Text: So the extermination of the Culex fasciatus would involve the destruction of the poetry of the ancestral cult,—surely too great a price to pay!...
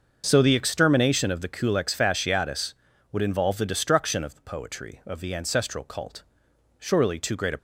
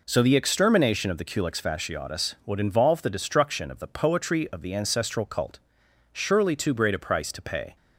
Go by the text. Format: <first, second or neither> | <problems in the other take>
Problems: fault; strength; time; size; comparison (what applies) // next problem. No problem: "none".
second | starts louder than the rest; until 1.2 s; 6.5 dB // stops before "price to pay"; at 7.5 s